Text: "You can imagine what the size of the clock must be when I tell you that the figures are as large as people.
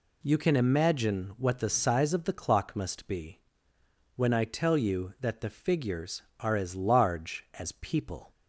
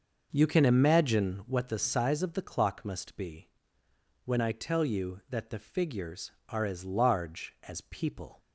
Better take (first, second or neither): first